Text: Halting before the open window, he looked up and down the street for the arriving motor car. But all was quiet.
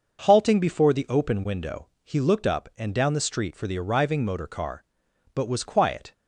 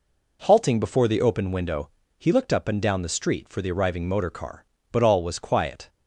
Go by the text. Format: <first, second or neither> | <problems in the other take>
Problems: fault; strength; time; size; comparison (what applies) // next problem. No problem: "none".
second | starts louder than the rest; noticeable; until 1.2 s; 6 dB // skips "all"; at 5.4 s